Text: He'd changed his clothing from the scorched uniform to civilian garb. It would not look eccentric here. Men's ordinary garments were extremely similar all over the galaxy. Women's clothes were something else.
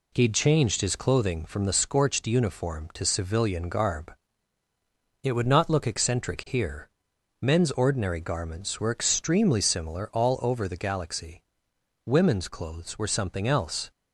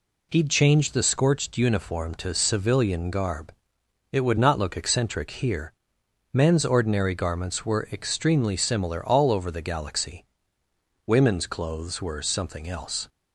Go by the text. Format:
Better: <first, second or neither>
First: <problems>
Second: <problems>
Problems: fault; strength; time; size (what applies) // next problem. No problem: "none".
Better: first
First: none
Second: skips "his clothing from"; at 0.9 s